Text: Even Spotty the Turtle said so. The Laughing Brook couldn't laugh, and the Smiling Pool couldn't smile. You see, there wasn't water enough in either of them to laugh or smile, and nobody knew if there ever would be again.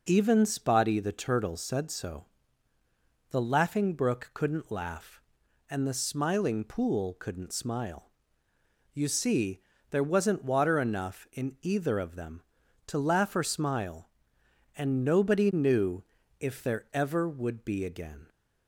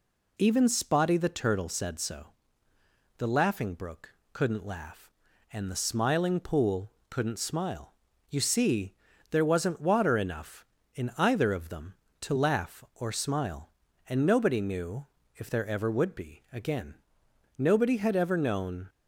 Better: first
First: pauses between "knew" and "if"; at 16.0 s; 0.38 s long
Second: pauses between "Brook" and "couldn't"; slight; at 4.1 s; 0.24 s long // pauses between "Pool" and "couldn't"; slight; at 6.9 s; 0.18 s long // pauses between "knew" and "if"; slight; at 15.0 s; 0.30 s long // goes on to say "Nobody had ever known"; noticeable; from 17.6 s on; 1.2 s long

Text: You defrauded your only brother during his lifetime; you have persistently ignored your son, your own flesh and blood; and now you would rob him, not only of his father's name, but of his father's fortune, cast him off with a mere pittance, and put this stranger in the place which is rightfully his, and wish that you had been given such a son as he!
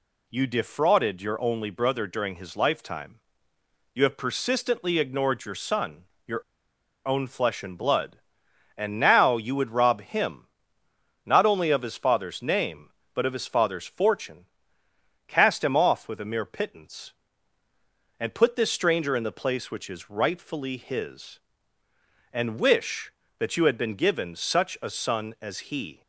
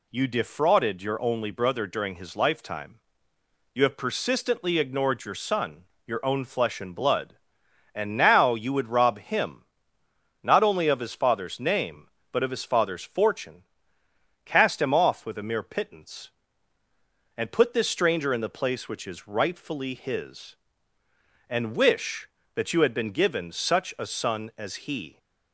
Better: second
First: pauses between "your" and "own"; noticeable; at 6.4 s; 0.64 s long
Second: none

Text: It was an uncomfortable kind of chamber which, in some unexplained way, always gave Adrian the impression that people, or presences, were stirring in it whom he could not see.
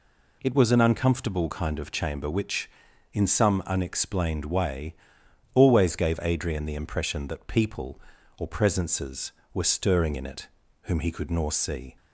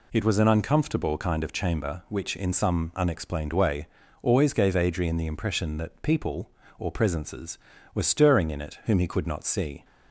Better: second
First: pauses between "it" and "whom"; slight; at 10.4 s; 0.34 s long // says "nor" for "not"; at 11.2 s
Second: none

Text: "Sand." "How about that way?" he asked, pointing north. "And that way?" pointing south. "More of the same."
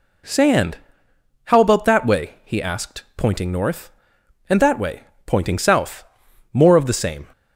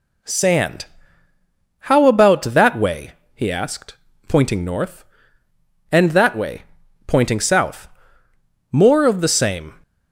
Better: neither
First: none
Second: none

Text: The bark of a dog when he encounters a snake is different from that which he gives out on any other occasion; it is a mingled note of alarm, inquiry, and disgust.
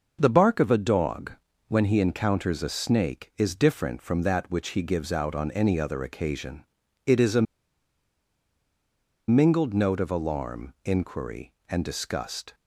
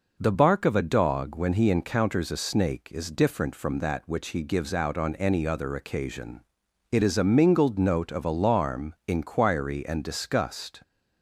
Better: second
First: pauses between "dog" and "when"; at 1.3 s; 0.38 s long // pauses between "a" and "mingled"; strong; at 7.4 s; 1.8 s long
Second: none

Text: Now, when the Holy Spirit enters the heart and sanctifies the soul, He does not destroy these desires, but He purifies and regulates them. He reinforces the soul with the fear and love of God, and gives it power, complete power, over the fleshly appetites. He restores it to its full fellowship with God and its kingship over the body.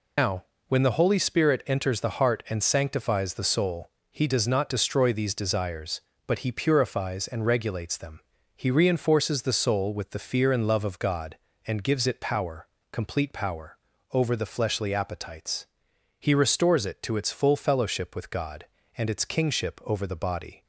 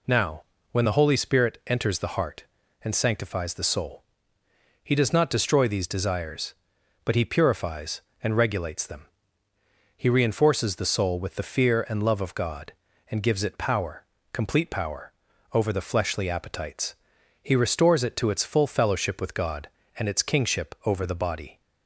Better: second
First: loses the start of "Now"; at 0.1 s; 120 ms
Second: none

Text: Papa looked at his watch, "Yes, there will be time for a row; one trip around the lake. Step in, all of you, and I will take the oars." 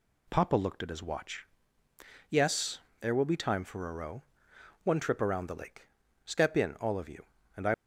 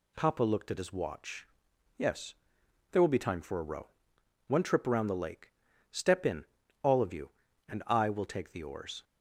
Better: second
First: stops before "will take the oars"; at 7.7 s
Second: none

